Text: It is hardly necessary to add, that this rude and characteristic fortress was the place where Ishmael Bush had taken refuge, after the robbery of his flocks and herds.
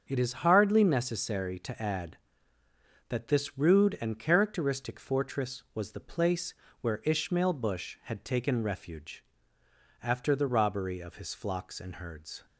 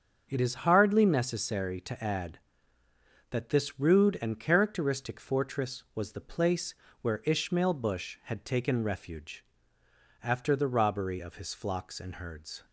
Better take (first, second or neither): neither